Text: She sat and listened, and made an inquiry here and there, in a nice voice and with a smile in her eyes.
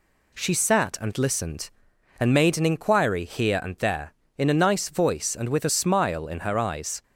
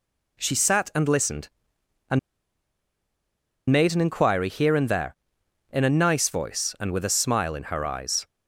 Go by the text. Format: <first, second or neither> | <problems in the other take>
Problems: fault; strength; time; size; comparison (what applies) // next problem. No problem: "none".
first | pauses between "and" and "made"; strong; at 2.1 s; 1.5 s long